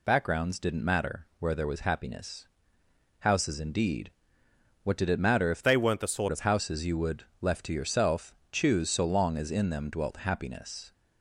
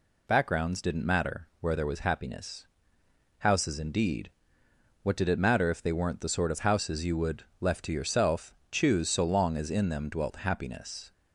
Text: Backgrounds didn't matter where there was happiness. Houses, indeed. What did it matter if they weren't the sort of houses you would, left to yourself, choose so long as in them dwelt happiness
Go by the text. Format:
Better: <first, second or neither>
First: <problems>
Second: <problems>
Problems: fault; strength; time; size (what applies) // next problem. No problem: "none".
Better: second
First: changes voice from "they" to "sort"; from 5.6 to 6.2 s; 0.6 s long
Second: none